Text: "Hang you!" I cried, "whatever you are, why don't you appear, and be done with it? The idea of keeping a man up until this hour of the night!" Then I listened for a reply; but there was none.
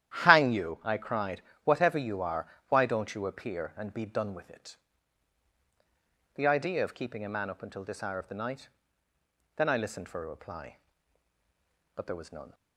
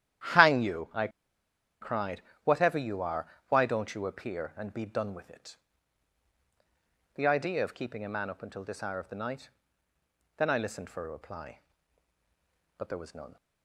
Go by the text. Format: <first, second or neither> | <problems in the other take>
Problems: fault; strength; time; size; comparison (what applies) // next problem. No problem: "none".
first | starts louder than the rest; strong; until 2.0 s; 11 dB; strong in the first // pauses between "I" and "cried"; noticeable; at 1.0 s; 0.73 s long